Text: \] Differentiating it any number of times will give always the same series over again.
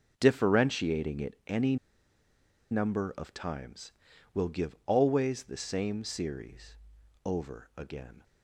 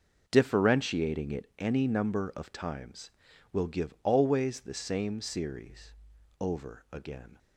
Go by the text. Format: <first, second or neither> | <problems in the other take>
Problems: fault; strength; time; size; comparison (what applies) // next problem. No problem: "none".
second | pauses between "any" and "number"; noticeable; at 1.7 s; 0.95 s long // pauses between "series" and "over"; noticeable; at 6.7 s; 0.48 s long; noticeable in the second